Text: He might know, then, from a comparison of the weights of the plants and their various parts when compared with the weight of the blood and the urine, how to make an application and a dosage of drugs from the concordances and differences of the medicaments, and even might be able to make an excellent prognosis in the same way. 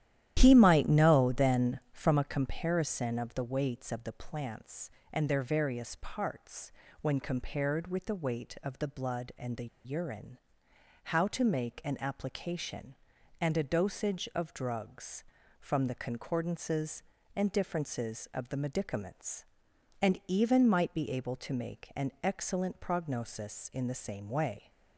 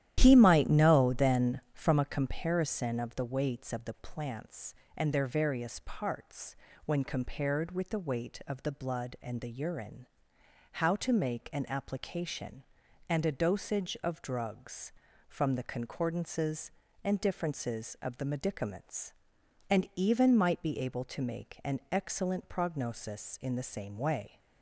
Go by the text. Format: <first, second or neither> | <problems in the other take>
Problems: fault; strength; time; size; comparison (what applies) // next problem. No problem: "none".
second | starts louder than the rest; strong; until 1.3 s; 11.5 dB; strong in the second // pauses between "parts" and "when"; slight; at 6.6 s; 0.32 s long; slight in the second // pauses between "the" and "urine"; slight; at 9.6 s; 0.18 s long